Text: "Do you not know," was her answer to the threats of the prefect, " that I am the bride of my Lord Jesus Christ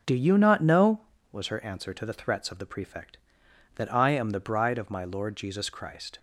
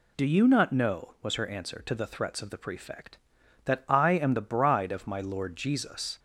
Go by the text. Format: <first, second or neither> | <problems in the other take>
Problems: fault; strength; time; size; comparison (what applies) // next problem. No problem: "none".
first | stops before "Christ"; at 6.1 s